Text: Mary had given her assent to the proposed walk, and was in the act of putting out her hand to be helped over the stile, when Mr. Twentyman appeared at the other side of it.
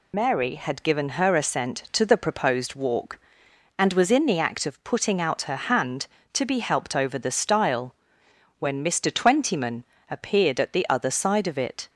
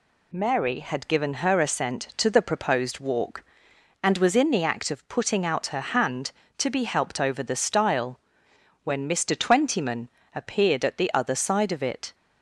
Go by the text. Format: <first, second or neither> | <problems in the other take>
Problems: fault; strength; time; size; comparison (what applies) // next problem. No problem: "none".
second | loses the start of "Mary"; at 0.1 s; 60 ms // pauses between "Twentyman" and "appeared"; slight; at 9.8 s; 0.26 s long; slight in the second